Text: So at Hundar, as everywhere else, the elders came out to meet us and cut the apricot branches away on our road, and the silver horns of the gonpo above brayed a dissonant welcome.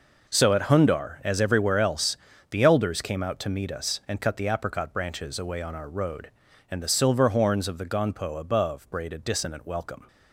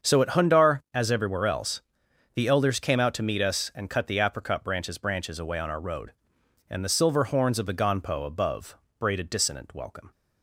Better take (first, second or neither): first